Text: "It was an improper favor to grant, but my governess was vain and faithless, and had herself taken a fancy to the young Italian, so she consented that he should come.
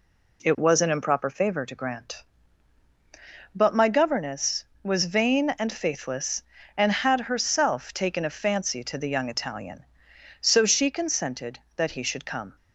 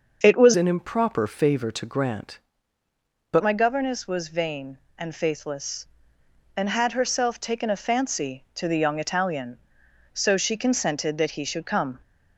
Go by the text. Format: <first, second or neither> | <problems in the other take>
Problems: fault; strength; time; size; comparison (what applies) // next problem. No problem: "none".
first | starts louder than the rest; until 1.2 s; 6 dB // changes voice from "an" to "but"; from 0.5 to 3.4 s; 2.9 s long